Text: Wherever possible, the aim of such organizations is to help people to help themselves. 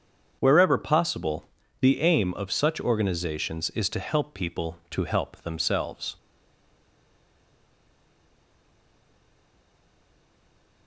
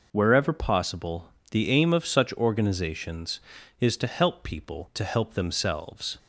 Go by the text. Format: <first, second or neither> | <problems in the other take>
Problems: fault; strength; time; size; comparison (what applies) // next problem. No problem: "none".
second | starts louder than the rest; until 1.4 s; 7 dB // stays silent after the last word; strong; from 6.1 s on; 4.7 s long